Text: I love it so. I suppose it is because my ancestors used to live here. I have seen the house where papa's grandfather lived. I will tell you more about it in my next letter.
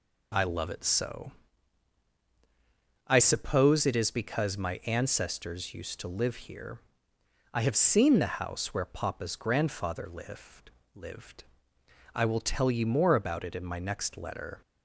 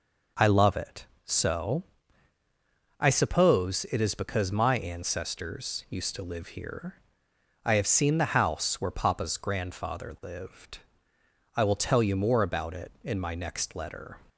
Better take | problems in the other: second | says "lived" twice; at 10.9 s

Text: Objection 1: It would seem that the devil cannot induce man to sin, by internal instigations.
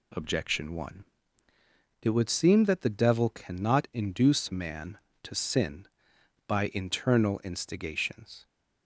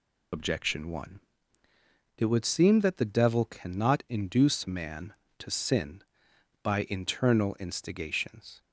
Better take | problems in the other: first | loses the start of "Objection"; at 0.3 s; 55 ms

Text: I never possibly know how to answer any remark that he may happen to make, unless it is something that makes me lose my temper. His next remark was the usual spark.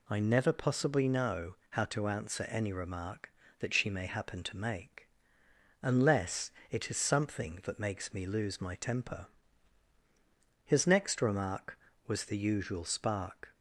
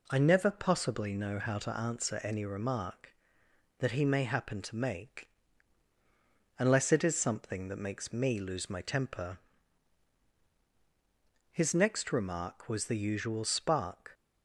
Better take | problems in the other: second | pauses between "know" and "how"; slight; at 1.5 s; 0.16 s long // says "she" for "he"; at 3.7 s // pauses between "unless" and "it"; slight; at 6.5 s; 0.18 s long

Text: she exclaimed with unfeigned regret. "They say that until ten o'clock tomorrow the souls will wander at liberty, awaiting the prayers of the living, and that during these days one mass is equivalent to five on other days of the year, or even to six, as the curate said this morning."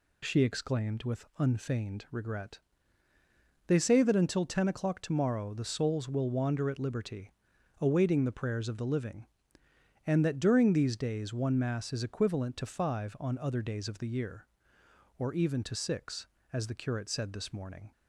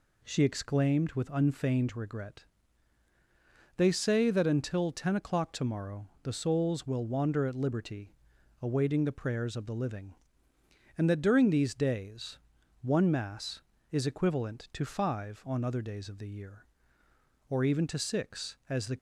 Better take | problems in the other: first | pauses between "days" and "one"; at 12.3 s; 0.42 s long // stops before "curate said this morning"; at 18.9 s

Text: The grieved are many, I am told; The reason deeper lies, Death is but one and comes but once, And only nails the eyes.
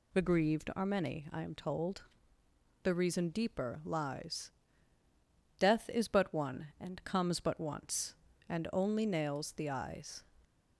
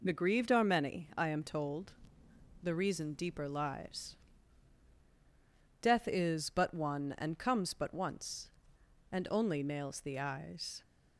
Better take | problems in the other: neither | none

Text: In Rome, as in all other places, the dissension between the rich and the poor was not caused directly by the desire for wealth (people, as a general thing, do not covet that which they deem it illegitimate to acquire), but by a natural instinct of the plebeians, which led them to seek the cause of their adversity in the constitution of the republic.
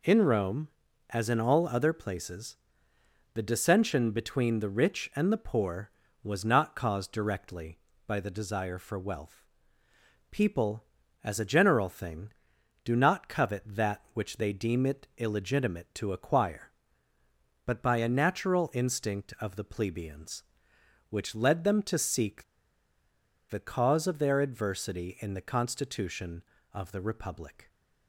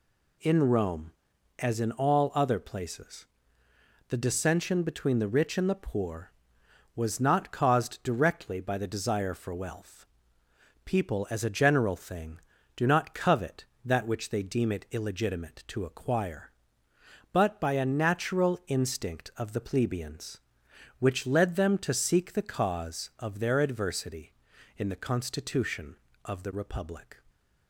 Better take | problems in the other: second | pauses between "seek" and "the"; at 22.4 s; 1.0 s long

